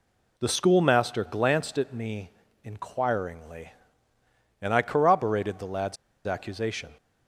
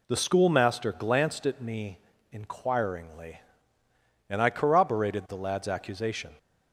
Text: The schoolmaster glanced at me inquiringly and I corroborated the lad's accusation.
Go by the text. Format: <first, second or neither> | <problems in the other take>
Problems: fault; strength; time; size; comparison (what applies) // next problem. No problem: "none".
second | pauses between "me" and "inquiringly"; slight; at 2.3 s; 0.32 s long; slight in the second // pauses between "lad's" and "accusation"; slight; at 5.9 s; 0.29 s long